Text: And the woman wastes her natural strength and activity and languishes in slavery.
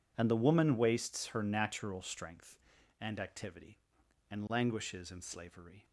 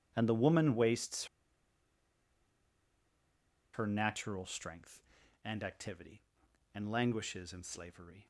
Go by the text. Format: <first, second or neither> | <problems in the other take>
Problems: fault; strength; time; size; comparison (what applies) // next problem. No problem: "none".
first | pauses between "wastes" and "her"; strong; at 1.2 s; 2.4 s long